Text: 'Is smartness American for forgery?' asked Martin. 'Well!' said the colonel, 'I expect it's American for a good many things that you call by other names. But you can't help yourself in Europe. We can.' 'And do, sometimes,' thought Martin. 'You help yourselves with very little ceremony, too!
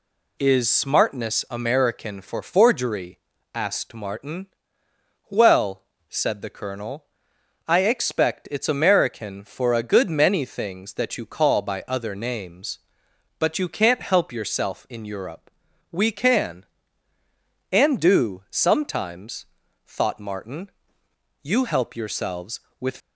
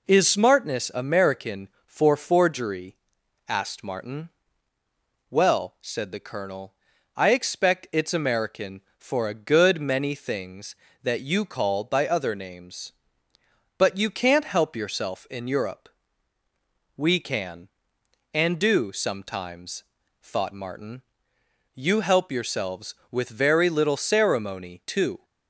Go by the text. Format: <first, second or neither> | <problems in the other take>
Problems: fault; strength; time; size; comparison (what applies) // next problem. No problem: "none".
second | stops before "very little ceremony too"; at 23.0 s